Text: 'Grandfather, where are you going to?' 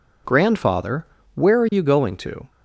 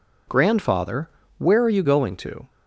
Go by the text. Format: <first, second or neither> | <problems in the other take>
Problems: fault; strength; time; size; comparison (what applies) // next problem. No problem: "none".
neither | none